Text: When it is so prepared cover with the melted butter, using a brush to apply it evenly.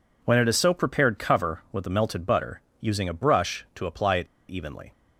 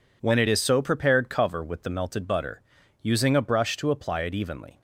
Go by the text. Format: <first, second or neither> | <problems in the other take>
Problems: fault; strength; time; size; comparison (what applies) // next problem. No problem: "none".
second | pauses between "it" and "evenly"; slight; at 4.2 s; 0.22 s long